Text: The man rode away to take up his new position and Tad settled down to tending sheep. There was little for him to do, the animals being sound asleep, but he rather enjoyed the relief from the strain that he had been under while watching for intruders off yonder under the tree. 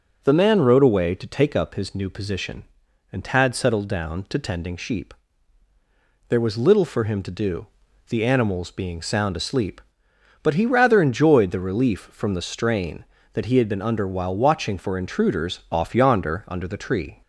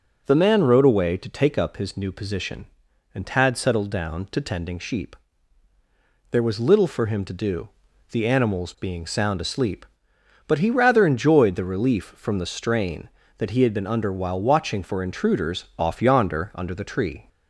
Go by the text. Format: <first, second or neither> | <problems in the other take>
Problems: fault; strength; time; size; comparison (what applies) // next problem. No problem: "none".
neither | none